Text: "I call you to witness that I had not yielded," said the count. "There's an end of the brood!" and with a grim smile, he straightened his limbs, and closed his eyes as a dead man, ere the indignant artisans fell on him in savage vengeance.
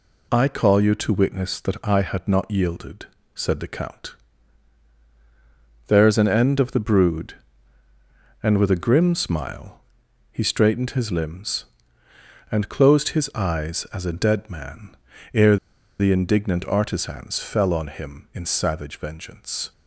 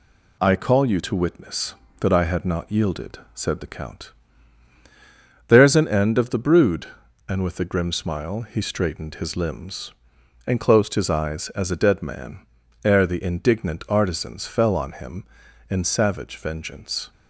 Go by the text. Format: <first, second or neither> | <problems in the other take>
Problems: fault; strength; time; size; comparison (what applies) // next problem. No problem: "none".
second | pauses between "ere" and "the"; at 15.5 s; 0.42 s long